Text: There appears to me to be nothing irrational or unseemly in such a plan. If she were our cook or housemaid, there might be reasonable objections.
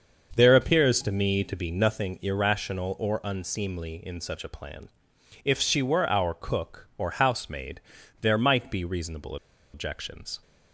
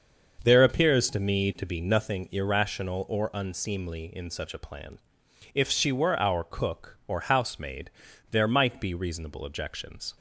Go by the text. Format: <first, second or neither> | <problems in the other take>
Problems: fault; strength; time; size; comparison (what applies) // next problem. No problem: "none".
second | starts louder than the rest; until 1.3 s; 6.5 dB; also in the second // pauses between "reasonable" and "objections"; at 9.3 s; 0.37 s long